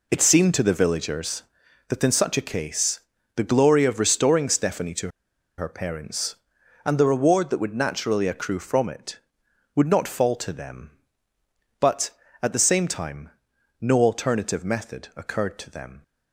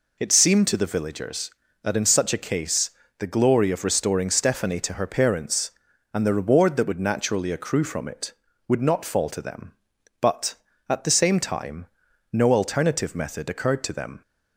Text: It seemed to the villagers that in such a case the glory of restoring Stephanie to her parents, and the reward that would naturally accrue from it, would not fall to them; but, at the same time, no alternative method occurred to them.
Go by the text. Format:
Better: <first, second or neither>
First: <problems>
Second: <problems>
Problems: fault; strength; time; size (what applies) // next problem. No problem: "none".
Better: second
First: pauses between "case" and "the"; slight; at 2.9 s; 0.36 s long // pauses between "to" and "her"; noticeable; at 5.0 s; 0.48 s long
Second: pauses between "case" and "the"; slight; at 2.8 s; 0.28 s long